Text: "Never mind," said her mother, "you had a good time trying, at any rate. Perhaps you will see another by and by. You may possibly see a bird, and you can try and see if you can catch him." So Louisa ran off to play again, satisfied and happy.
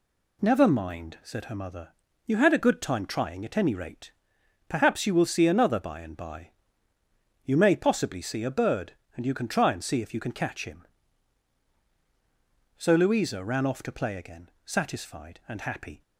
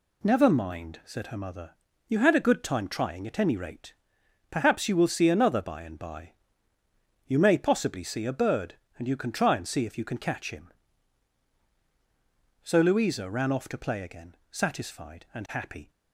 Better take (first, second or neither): neither